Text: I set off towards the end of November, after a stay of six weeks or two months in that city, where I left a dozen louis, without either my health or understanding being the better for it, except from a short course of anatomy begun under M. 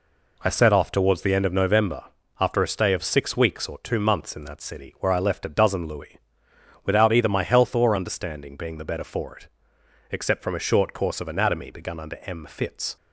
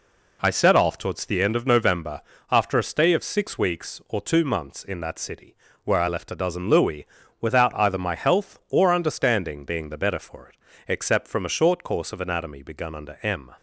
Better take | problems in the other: second | goes on to say "Fitz"; from 12.4 s on; 0.50 s long

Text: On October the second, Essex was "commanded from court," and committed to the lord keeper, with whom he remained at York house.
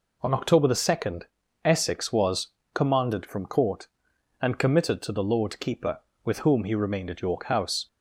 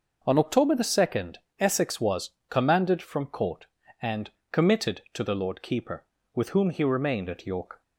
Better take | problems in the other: first | pauses between "was" and "commanded"; slight; at 2.2 s; 0.18 s long; slight in the first // pauses between "and" and "committed"; slight; at 4.2 s; 0.22 s long // stops before "house"; at 7.8 s

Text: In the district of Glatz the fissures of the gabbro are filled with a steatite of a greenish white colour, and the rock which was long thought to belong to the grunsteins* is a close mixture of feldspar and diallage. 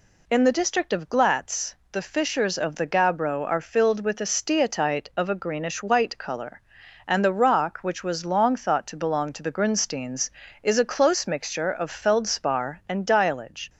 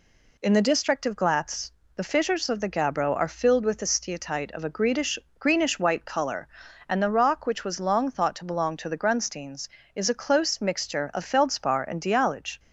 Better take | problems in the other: first | pauses between "Glatz" and "the"; slight; at 1.7 s; 0.24 s long; slight in the first // says "greenish" twice; at 5.3 s

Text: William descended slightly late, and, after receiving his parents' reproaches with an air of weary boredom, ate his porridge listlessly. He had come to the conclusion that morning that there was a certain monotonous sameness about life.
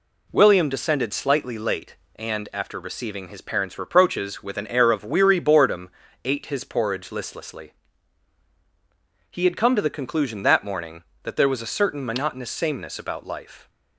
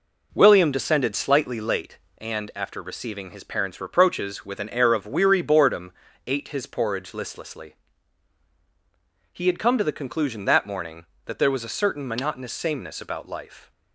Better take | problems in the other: first | starts louder than the rest; noticeable; until 1.9 s; 4.5 dB

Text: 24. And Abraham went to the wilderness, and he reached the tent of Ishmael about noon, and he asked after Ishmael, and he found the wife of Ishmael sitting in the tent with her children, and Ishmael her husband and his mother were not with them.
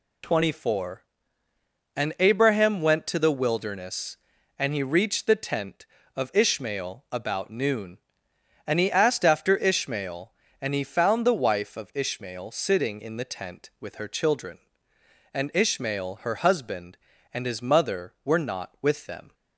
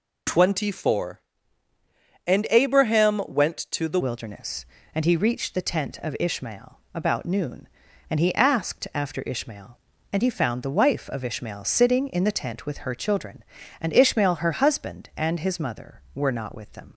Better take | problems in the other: first | changes voice at "wilderness"; from 4.0 s on; 12.9 s long

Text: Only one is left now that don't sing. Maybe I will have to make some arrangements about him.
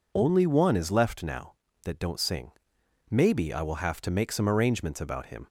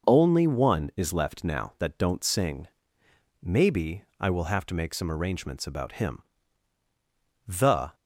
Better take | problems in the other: first | pauses between "Maybe" and "I"; slight; at 4.0 s; 0.18 s long // goes on to say "The"; slight; from 7.4 s on; 0.48 s long

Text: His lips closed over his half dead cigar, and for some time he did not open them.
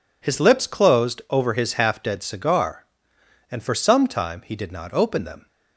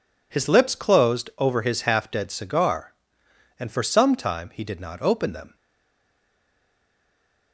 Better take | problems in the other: first | stays silent after the last word; noticeable; from 5.5 s on; 2.0 s long

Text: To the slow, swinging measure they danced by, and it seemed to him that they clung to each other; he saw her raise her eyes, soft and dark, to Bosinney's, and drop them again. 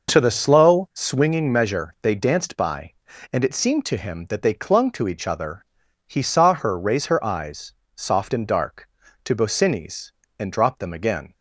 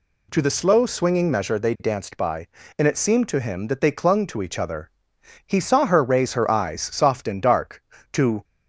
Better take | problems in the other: first | stops before "Bosinney's and drop them again"; at 8.4 s

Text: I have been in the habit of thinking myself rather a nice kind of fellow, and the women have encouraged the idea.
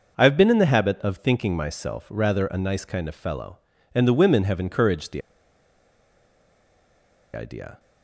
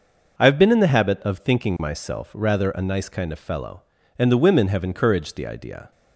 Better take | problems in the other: second | pauses between "the" and "idea"; strong; at 5.2 s; 2.1 s long

